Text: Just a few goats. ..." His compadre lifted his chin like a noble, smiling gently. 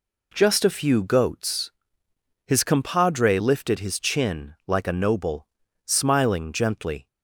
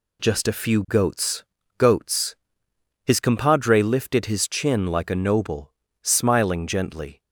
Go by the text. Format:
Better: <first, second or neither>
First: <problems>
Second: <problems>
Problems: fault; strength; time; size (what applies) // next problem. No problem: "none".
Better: first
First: none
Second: says "goats" twice; at 1.7 s